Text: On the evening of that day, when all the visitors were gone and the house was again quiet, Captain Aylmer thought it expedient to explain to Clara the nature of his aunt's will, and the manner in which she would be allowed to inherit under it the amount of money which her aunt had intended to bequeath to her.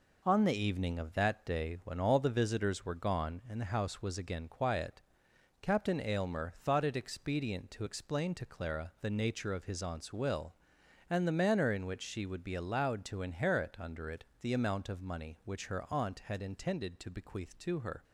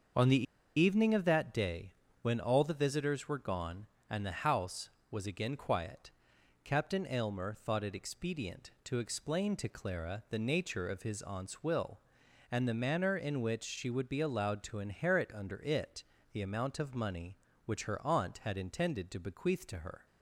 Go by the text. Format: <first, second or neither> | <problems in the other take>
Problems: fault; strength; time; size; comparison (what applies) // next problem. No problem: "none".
first | starts louder than the rest; until 1.5 s; 6.5 dB // pauses between "the" and "evening"; slight; at 0.4 s; 0.34 s long // pauses between "it" and "the"; slight; at 16.0 s; 0.32 s long; slight in the first